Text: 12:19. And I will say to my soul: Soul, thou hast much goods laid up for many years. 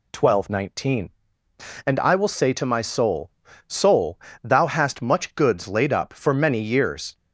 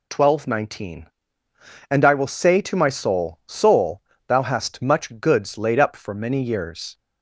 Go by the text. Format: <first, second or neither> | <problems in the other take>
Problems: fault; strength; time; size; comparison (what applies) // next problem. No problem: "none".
neither | none